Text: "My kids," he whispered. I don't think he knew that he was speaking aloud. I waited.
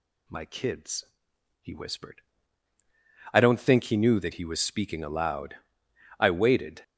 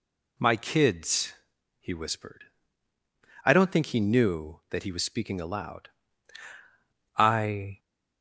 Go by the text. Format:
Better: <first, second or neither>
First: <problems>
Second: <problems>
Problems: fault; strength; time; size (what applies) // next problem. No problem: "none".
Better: first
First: none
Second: stops before "waited"; at 7.7 s